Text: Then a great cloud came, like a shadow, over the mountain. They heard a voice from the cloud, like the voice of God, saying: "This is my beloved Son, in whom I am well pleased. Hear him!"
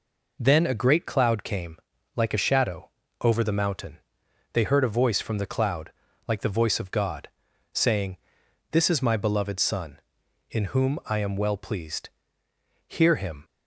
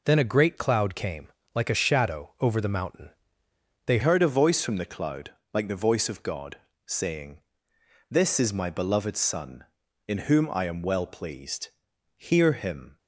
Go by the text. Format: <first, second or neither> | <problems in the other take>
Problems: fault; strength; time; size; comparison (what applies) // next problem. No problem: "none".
first | changes voice at "heard"; from 4.0 s on; 8.9 s long